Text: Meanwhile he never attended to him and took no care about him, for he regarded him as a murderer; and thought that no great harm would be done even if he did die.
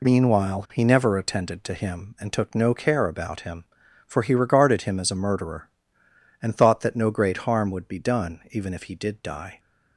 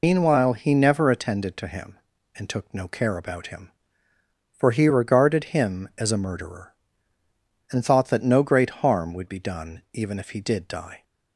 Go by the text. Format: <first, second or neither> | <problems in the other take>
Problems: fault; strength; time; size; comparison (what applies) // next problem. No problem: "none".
first | loses the start of "Meanwhile"; at 0.0 s; 115 ms